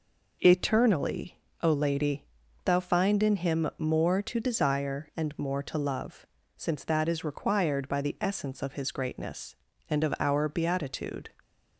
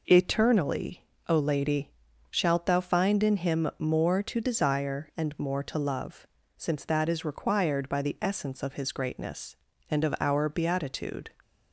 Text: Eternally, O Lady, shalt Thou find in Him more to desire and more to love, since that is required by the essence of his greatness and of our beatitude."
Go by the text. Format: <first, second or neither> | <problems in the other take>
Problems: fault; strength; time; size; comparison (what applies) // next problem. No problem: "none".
second | skips "shalt"; at 2.4 s